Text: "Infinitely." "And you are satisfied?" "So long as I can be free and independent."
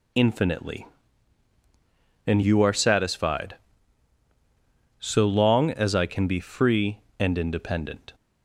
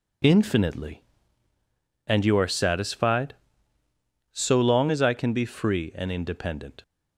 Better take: neither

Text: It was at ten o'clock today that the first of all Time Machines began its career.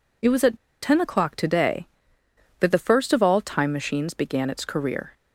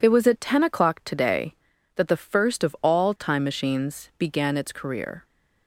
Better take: second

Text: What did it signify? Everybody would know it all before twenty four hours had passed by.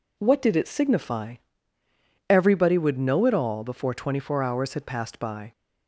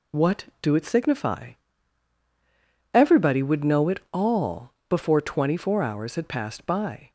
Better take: first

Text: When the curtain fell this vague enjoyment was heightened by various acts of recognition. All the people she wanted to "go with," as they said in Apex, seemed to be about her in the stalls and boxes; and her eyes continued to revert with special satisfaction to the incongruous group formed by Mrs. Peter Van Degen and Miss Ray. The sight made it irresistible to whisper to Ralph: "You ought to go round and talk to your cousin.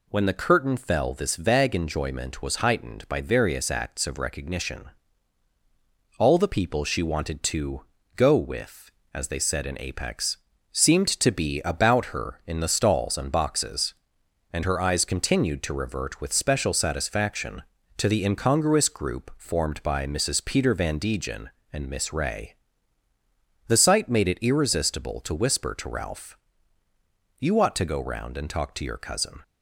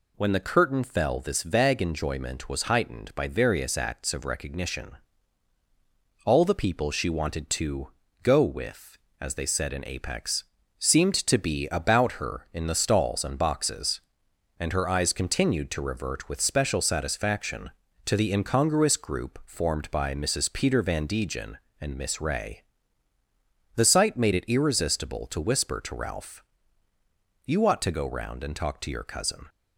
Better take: neither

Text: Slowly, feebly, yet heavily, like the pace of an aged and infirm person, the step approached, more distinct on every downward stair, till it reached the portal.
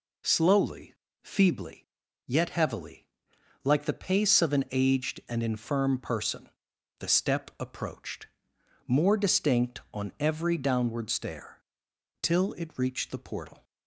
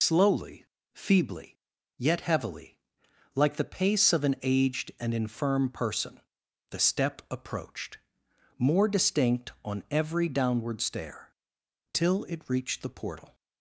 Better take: first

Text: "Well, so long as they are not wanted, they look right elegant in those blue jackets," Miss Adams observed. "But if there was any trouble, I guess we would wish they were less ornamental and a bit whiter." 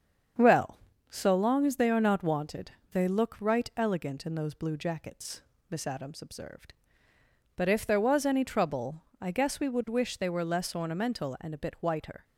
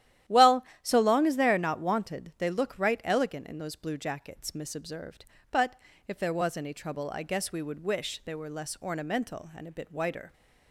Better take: first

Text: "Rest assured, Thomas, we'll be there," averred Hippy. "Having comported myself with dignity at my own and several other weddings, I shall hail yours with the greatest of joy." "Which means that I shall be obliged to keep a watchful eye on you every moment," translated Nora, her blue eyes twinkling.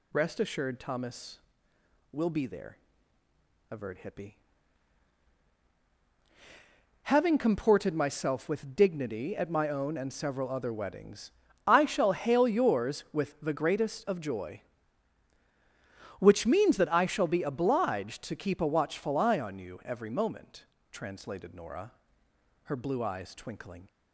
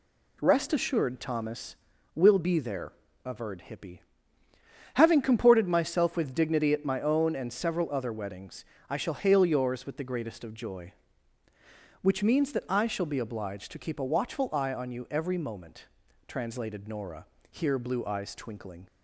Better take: first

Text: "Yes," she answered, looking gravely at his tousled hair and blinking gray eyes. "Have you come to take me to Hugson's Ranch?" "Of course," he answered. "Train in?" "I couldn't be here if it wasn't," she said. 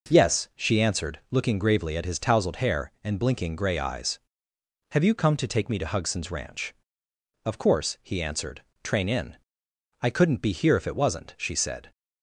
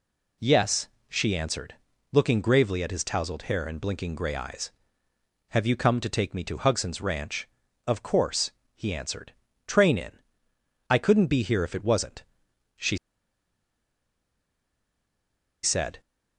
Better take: first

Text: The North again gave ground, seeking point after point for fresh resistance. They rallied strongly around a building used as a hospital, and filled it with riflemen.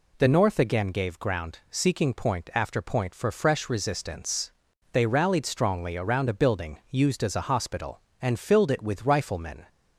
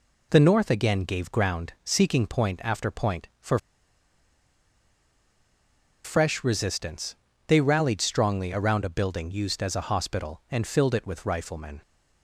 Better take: first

